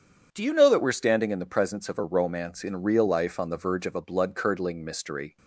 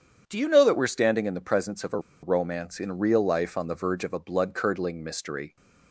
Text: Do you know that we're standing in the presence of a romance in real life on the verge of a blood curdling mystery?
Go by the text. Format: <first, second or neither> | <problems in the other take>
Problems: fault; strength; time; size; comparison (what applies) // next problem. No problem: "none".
first | starts louder than the rest; strong; until 1.2 s; 8 dB; strong in the first // pauses between "a" and "romance"; slight; at 1.9 s; 0.23 s long